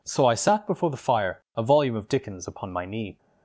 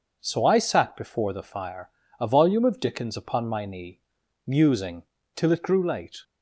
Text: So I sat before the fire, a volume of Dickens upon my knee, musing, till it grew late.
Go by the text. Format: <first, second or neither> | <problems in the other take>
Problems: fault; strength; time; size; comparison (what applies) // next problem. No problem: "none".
second | stops before "musing till it grew late"; at 3.1 s